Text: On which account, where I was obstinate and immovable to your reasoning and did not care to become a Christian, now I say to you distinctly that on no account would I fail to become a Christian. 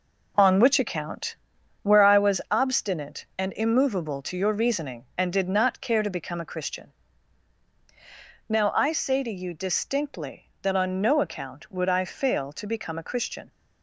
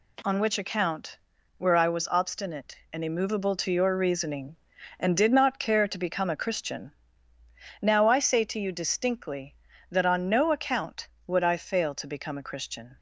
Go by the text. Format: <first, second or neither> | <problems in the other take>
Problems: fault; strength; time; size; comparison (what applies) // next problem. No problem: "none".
second | gets quieter; strong; throughout; 8 dB